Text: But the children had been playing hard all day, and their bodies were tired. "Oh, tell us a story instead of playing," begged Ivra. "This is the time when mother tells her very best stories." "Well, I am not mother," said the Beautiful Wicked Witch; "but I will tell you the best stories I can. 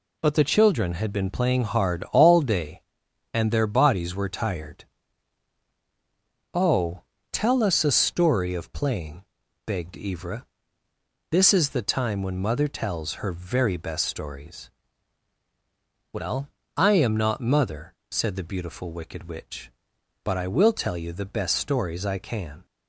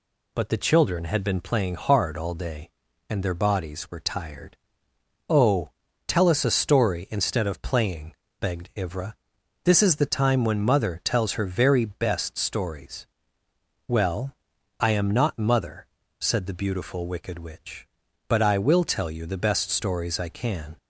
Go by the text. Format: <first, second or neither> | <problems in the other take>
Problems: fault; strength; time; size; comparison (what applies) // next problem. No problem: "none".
second | skips "instead"; at 8.5 s